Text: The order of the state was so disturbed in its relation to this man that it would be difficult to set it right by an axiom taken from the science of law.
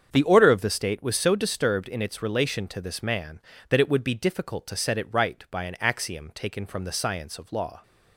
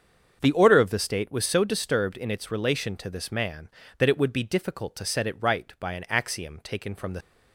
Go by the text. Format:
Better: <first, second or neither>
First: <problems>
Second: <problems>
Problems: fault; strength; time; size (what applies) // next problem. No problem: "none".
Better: first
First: starts louder than the rest; strong; until 1.1 s; 7.5 dB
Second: starts louder than the rest; until 1.4 s; 7 dB // stops before "science of law"; at 7.2 s